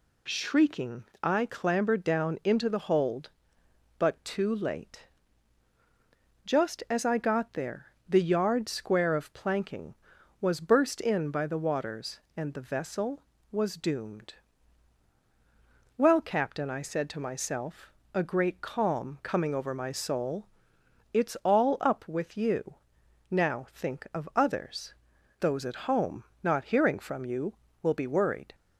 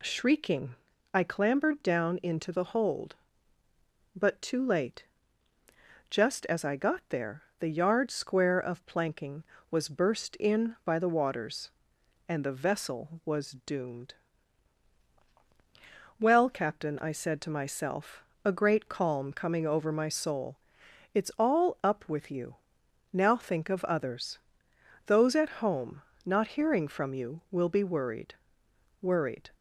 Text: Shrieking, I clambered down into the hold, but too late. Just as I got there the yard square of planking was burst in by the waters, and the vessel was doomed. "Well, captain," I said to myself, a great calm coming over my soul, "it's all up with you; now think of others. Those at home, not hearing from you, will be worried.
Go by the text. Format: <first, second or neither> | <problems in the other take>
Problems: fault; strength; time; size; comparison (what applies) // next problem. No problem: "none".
first | pauses between "there" and "the"; slight; at 7.4 s; 0.16 s long; slight in the first // says "worried" twice; at 28.9 s